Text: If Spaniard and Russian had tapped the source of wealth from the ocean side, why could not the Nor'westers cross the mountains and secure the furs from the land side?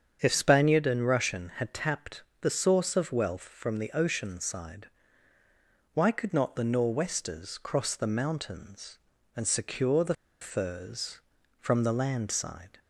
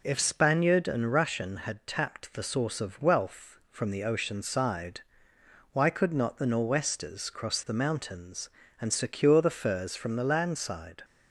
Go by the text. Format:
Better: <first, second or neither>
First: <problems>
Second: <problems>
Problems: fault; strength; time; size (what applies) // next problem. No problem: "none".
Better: second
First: starts louder than the rest; strong; until 1.2 s; 7.5 dB // pauses between "tapped" and "the"; slight; at 2.2 s; 0.20 s long // pauses between "the" and "furs"; slight; at 10.1 s; 0.27 s long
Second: none